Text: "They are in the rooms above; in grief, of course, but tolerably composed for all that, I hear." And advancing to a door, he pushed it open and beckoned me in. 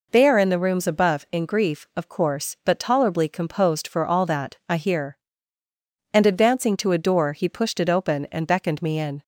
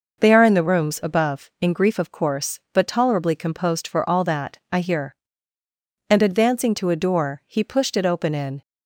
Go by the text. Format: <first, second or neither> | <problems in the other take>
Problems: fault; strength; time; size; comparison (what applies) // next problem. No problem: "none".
first | skips "and beckoned me"; at 8.3 s